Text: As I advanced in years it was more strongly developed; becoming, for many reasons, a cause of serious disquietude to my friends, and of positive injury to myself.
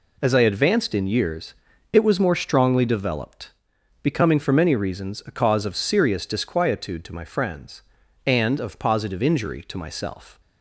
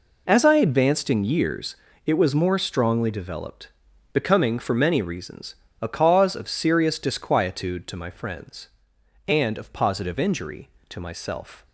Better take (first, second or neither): neither